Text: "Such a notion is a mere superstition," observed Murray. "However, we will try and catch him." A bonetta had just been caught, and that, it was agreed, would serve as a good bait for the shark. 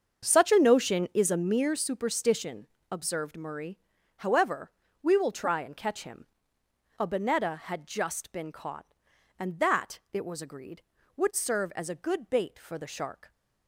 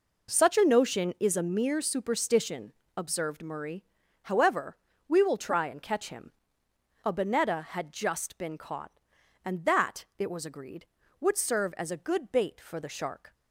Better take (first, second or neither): second